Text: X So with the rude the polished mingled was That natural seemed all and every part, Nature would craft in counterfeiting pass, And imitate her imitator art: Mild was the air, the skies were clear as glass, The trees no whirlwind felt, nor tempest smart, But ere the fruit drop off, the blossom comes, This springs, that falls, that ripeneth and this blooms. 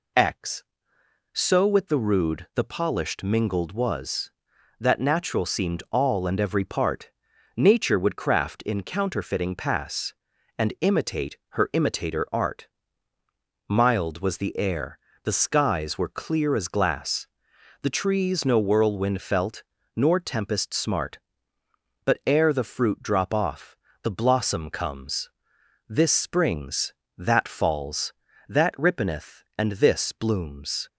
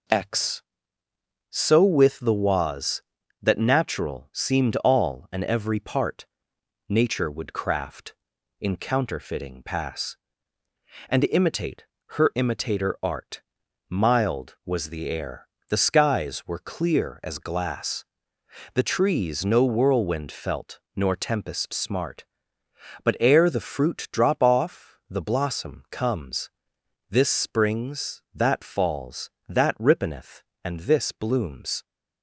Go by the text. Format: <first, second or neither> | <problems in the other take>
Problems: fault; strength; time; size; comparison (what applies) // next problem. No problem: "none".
first | skips "rude the polished mingled"; at 2.3 s // pauses between "imitate" and "her"; slight; at 11.8 s; 0.26 s long